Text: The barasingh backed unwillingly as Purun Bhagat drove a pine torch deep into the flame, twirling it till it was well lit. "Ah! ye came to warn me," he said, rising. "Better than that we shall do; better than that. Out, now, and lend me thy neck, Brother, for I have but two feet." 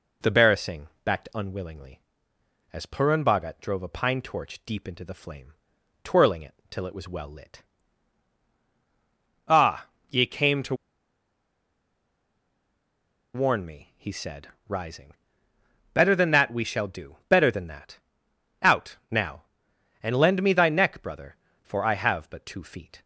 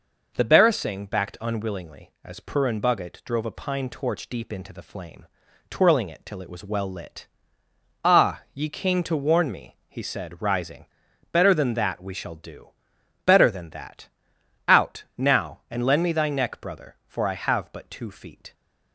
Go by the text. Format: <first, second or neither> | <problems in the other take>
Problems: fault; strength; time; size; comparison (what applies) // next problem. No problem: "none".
second | pauses between "barasingh" and "backed"; slight; at 0.8 s; 0.18 s long // pauses between "it" and "till"; slight; at 6.5 s; 0.16 s long // pauses between "to" and "warn"; strong; at 10.7 s; 2.6 s long